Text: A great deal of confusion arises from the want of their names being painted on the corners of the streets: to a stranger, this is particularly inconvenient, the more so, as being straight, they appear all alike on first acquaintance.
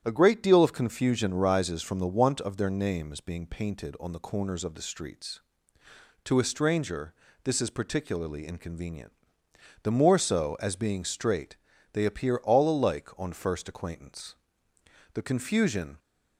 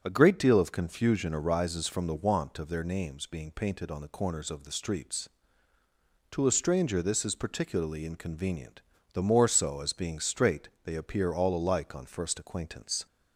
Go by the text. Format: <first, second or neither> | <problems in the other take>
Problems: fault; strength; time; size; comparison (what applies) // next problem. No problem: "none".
second | starts louder than the rest; strong; until 1.0 s; 9.5 dB; strong in the second // goes on to say "The confusion"; noticeable; from 15.1 s on; 0.86 s long